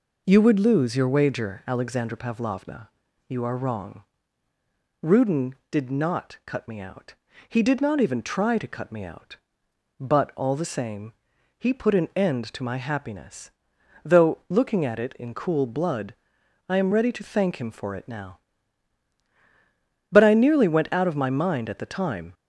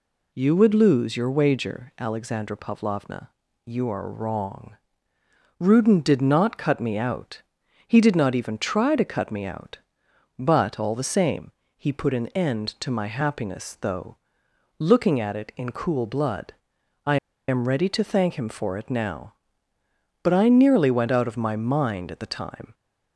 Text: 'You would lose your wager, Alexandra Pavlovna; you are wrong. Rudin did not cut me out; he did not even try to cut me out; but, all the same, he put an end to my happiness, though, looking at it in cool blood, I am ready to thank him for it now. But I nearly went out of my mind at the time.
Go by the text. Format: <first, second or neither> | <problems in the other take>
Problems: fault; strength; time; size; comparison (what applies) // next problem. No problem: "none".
first | pauses between "I" and "am"; slight; at 17.1 s; 0.32 s long